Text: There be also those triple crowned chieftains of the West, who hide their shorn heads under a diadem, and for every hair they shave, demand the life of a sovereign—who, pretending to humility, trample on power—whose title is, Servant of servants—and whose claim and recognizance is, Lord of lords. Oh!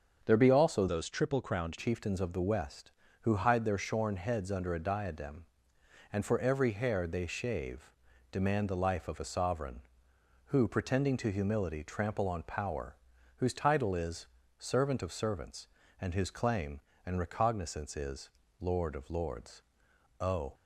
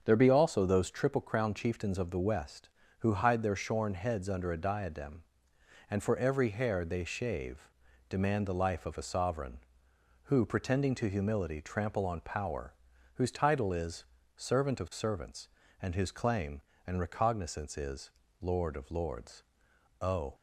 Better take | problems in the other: second | starts louder than the rest; until 1.2 s; 7 dB; also in the second // changes voice from "those" to "crowned"; from 0.8 to 1.7 s; 0.9 s long

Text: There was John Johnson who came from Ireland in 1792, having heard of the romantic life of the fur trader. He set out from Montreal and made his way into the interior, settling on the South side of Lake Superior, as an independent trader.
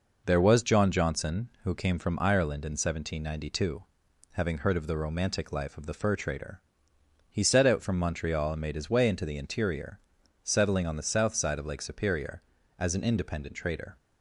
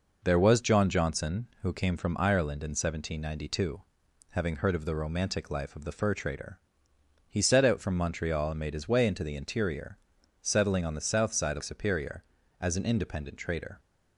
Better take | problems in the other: first | skips "Lake"; at 11.6 s

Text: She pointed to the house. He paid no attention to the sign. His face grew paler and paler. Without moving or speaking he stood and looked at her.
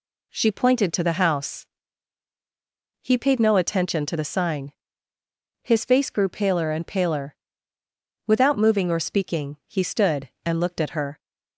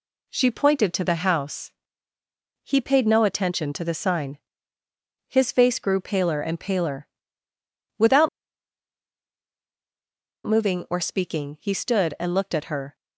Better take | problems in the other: first | pauses between "Without" and "moving"; strong; at 8.2 s; 2.1 s long

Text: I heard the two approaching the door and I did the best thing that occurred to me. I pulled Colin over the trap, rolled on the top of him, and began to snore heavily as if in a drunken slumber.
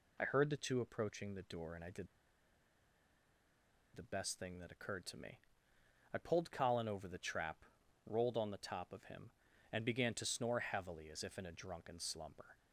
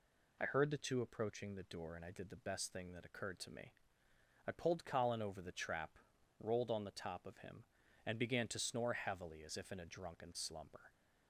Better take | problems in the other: second | pauses between "did" and "the"; strong; at 2.0 s; 1.8 s long

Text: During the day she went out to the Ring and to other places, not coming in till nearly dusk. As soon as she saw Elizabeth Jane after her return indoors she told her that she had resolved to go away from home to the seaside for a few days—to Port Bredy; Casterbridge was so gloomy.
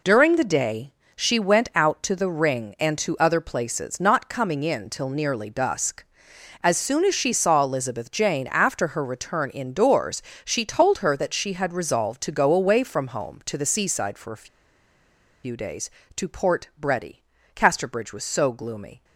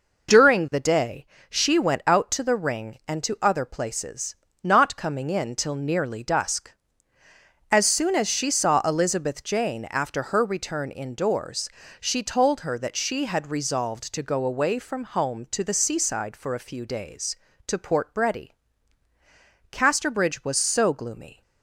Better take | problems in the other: second | pauses between "day" and "she"; slight; at 0.9 s; 0.22 s long; slight in the second // pauses between "indoors" and "she"; slight; at 10.2 s; 0.22 s long; slight in the second // pauses between "a" and "few"; noticeable; at 14.4 s; 0.97 s long

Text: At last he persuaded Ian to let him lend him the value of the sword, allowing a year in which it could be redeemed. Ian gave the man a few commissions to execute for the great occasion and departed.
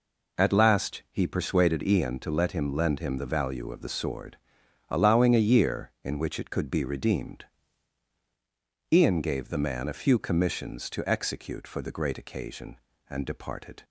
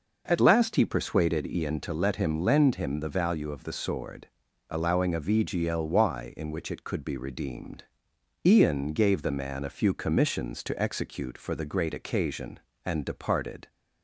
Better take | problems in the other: first | says "vgly" for "year"; at 5.2 s

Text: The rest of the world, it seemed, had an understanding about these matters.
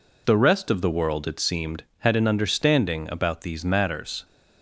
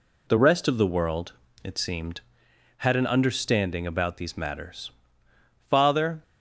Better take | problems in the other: first | goes on to say "Father"; from 5.7 s on; 0.52 s long

